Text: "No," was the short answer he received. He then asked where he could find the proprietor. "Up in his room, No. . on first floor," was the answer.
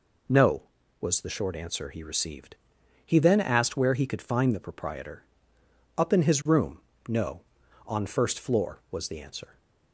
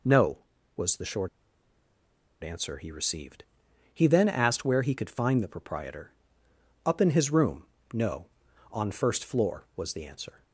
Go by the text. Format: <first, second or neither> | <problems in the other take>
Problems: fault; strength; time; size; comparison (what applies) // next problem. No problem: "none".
first | pauses between "short" and "answer"; at 1.2 s; 1.1 s long